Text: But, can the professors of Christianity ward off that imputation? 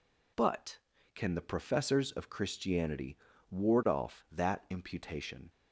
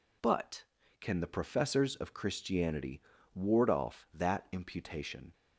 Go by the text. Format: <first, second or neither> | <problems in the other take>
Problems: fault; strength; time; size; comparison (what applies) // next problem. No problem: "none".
neither | pauses between "Christianity" and "ward"; slight; the same in both